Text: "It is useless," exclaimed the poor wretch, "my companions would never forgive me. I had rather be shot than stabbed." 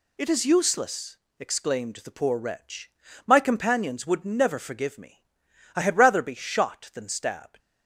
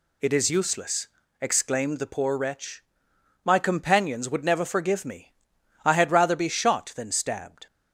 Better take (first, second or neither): second